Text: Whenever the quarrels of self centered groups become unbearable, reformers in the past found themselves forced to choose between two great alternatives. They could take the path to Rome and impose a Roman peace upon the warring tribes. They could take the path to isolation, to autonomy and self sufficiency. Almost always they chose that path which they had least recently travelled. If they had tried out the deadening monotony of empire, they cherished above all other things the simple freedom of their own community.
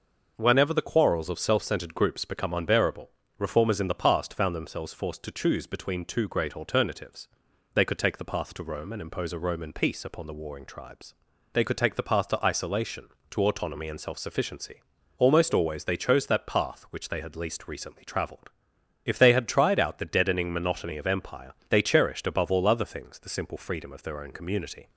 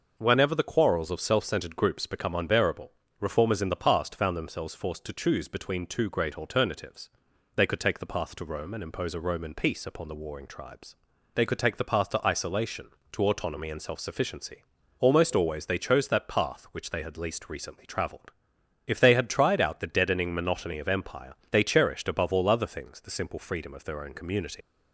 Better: first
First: none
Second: leaves "community" unfinished; at 24.6 s; 105 ms

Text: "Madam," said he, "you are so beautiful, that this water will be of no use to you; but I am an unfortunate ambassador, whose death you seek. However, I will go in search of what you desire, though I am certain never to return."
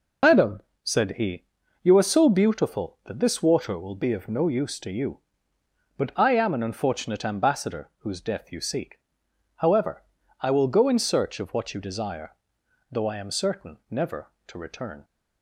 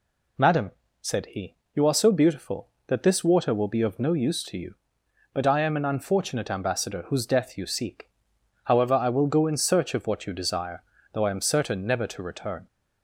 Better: second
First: loses the start of "Madam"; at 0.2 s; 130 ms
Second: none

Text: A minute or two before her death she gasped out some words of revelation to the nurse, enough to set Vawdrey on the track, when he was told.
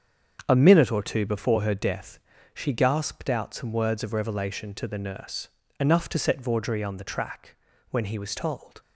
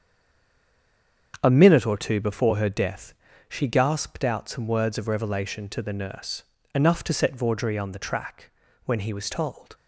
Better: first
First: starts louder than the rest; strong; until 1.4 s; 7.5 dB // pauses between "death" and "she"; slight; at 2.1 s; 0.36 s long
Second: stays silent before the first word; noticeable; until 1.3 s; 1.3 s long // starts louder than the rest; strong; until 2.4 s; 7.5 dB // pauses between "death" and "she"; slight; at 3.1 s; 0.36 s long

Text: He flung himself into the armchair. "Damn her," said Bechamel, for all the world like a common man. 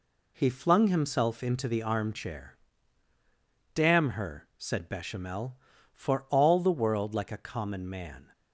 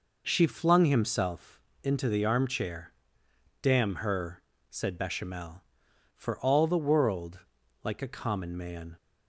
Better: first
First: none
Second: says "She" for "He"; at 0.2 s // pauses between "himself" and "into"; slight; at 1.5 s; 0.24 s long // pauses between "world" and "like"; at 7.4 s; 0.41 s long

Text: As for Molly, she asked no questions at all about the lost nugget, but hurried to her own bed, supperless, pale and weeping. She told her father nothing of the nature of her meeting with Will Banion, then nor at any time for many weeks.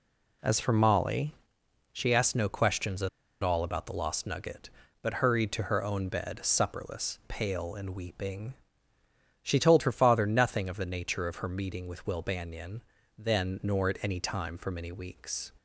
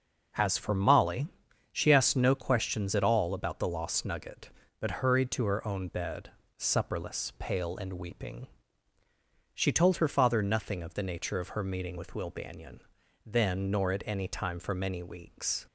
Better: second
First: pauses between "at" and "all"; slight; at 3.0 s; 0.33 s long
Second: none

